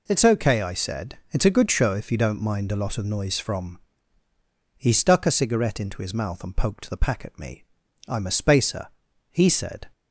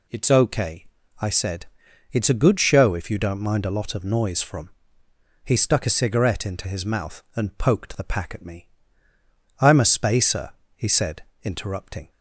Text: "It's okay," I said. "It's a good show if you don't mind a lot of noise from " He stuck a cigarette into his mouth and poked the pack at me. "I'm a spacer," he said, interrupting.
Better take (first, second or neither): second